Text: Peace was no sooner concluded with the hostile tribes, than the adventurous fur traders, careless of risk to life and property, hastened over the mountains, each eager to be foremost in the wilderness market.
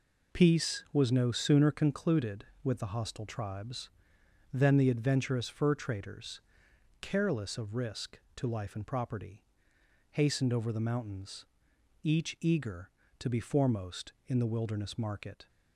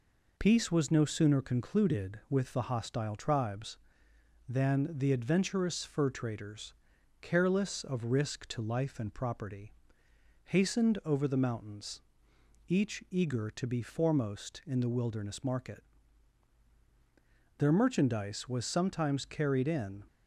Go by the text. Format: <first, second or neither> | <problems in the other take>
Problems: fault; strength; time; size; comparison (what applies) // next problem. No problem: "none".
first | goes on to say "Their merchandise was sometimes carried in"; strong; from 17.5 s on; 2.4 s long